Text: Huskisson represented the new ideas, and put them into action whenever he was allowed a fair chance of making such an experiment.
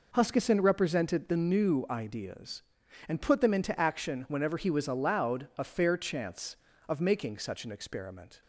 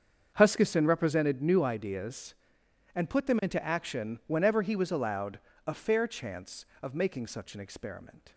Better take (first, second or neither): first